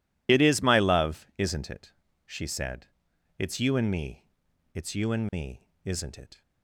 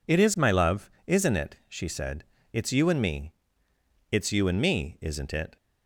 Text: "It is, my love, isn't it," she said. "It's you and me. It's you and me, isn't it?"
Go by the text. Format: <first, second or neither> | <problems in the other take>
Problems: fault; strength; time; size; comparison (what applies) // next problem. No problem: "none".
second | loses the start of "It"; at 0.2 s; 30 ms